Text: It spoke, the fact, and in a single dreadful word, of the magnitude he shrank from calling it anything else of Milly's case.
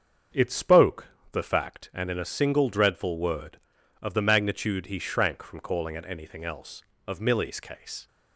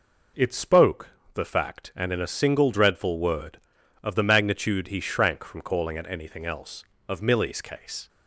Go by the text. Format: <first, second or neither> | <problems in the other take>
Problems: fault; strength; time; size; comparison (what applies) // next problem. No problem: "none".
second | starts louder than the rest; until 1.8 s; 7 dB